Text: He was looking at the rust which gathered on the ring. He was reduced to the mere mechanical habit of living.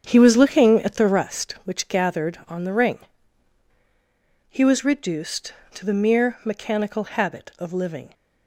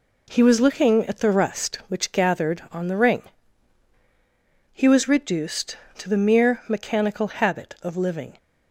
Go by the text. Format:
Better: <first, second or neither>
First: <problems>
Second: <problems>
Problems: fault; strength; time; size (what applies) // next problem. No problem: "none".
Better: second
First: starts louder than the rest; strong; until 1.2 s; 8 dB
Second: none